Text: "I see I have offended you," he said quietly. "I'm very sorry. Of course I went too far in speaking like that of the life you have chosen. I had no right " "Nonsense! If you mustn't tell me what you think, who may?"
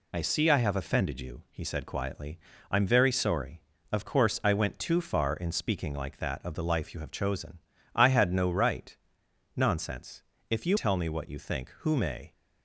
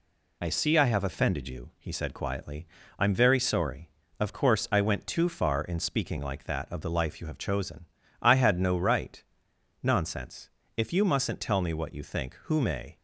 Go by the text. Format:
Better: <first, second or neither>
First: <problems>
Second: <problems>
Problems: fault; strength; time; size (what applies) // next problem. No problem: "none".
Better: second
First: skips "mustn't"; at 10.7 s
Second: none